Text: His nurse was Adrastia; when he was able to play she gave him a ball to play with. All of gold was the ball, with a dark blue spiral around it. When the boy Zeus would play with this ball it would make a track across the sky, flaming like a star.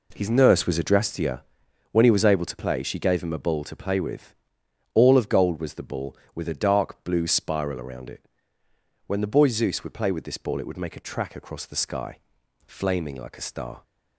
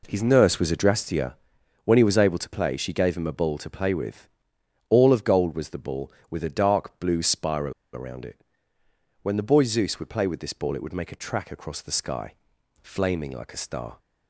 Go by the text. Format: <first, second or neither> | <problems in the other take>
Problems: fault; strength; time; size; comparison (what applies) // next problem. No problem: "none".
first | pauses between "spiral" and "around"; slight; at 7.7 s; 0.21 s long